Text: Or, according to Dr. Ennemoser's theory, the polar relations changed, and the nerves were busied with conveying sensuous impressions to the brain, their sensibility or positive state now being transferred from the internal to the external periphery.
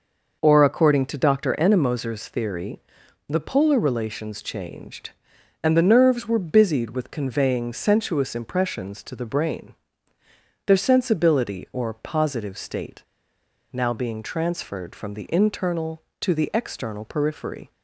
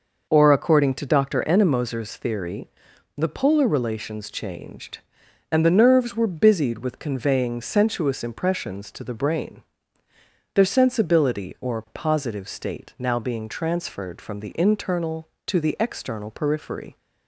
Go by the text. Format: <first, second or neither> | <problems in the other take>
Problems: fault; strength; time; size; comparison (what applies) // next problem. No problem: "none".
second | pauses between "state" and "now"; noticeable; at 13.0 s; 0.70 s long